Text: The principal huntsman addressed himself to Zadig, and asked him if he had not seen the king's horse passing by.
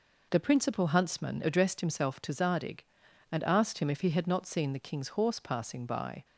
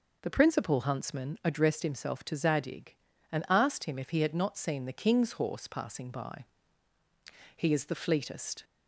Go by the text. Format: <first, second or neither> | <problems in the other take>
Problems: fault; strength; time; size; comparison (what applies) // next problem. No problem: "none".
first | goes on to say "He is the fleetest"; noticeable; from 7.5 s on; 1.0 s long